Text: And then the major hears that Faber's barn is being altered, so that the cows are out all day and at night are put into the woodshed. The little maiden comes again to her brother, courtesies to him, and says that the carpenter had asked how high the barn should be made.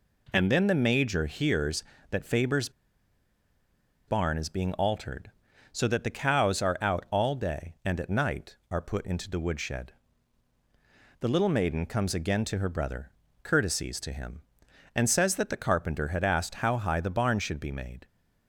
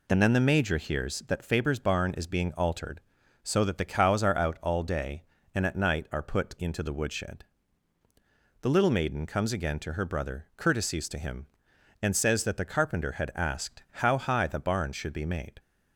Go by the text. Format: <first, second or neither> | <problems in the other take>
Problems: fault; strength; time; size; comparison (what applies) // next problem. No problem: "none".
second | pauses between "Faber's" and "barn"; strong; at 2.6 s; 1.3 s long